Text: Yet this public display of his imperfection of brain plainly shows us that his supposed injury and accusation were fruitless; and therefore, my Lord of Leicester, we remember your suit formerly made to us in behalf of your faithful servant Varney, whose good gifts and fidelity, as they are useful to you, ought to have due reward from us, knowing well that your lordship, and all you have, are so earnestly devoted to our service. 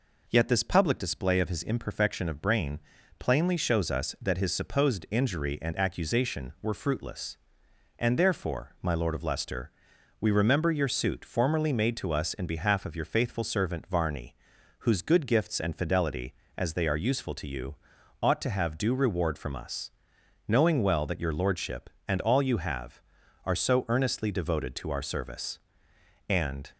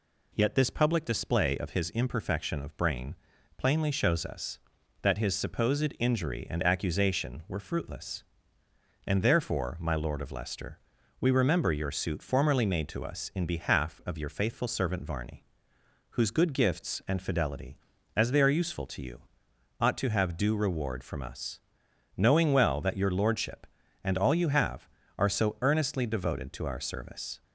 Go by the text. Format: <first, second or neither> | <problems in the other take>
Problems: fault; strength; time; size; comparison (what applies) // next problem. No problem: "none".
second | pauses between "brain" and "plainly"; at 2.7 s; 0.40 s long; also in the second // goes on to say "And"; slight; from 26.2 s on; 0.42 s long